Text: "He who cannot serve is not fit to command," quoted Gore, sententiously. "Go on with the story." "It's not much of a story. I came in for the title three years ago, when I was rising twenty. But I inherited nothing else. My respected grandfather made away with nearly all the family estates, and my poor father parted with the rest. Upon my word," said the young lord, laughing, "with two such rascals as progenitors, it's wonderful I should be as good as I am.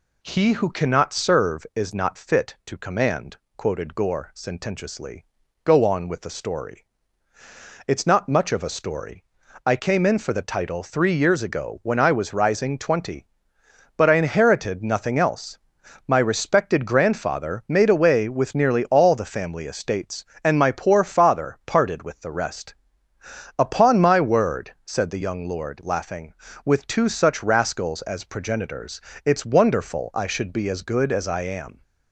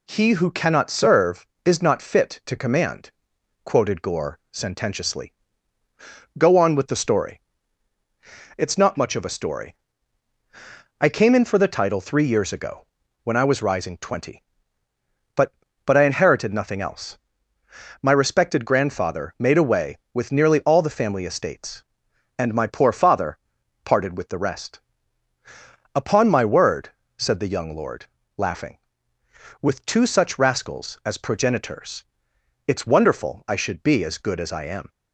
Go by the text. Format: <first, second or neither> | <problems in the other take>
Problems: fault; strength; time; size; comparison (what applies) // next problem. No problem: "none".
first | says "But" twice; at 15.8 s // pauses between "father" and "parted"; noticeable; at 23.3 s; 0.46 s long